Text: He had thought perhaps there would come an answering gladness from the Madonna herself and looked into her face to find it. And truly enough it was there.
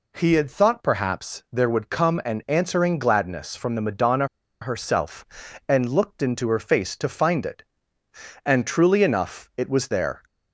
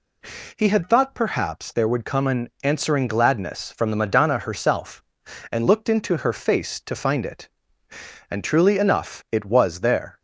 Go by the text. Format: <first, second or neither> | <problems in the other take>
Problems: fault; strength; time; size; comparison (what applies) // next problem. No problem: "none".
second | pauses between "Madonna" and "herself"; at 4.2 s; 0.36 s long